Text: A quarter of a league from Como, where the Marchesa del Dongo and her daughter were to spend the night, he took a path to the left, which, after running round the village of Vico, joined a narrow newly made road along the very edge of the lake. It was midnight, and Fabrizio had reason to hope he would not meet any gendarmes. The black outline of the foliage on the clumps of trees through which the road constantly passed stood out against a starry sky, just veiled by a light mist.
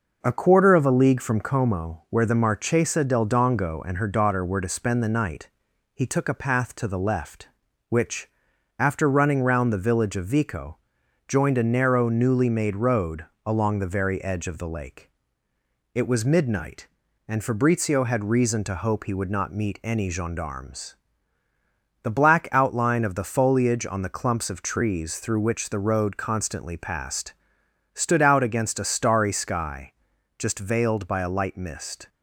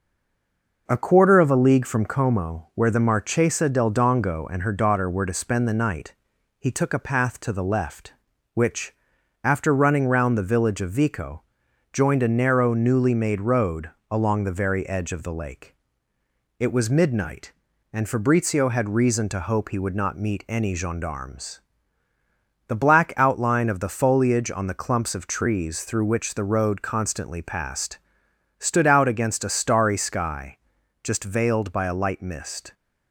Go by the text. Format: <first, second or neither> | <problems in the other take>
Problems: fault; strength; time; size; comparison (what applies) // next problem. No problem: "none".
first | stays silent before the first word; slight; until 0.8 s; 0.8 s long // pauses between "road" and "along"; slight; at 13.8 s; 0.22 s long; slight in the first // pauses between "passed" and "stood"; noticeable; at 27.9 s; 0.62 s long; noticeable in the first